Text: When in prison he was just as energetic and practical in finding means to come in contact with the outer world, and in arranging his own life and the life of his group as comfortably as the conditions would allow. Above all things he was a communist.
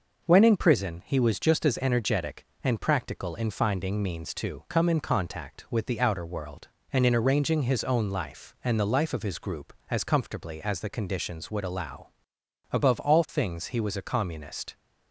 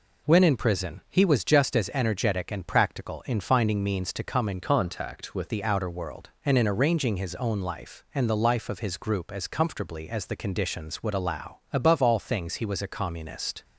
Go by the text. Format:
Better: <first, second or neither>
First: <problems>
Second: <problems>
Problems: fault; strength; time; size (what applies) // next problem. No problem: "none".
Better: first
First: none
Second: changes voice from "contact" to "with"; from 4.6 to 5.4 s; 0.8 s long